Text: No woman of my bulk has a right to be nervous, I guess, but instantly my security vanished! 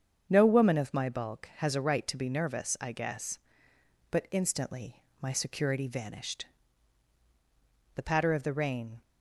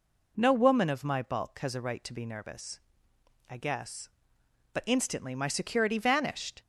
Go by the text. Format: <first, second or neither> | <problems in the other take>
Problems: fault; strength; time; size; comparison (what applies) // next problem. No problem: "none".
second | starts louder than the rest; until 1.3 s; 7 dB // pauses between "instantly" and "my"; slight; at 5.0 s; 0.18 s long // goes on to say "The patter of the rain"; noticeable; from 7.9 s on; 1.0 s long